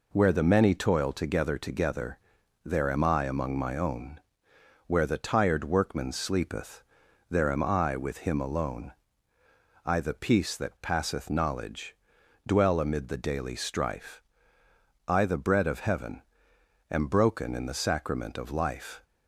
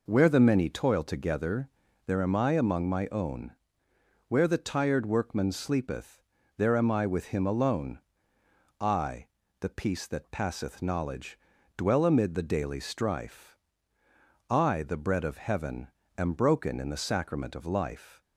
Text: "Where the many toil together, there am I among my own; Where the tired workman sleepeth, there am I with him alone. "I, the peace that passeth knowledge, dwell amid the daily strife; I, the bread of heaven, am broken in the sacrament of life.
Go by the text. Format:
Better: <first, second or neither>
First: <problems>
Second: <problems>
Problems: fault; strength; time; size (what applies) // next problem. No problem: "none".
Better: second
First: says "together" twice; at 1.5 s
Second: none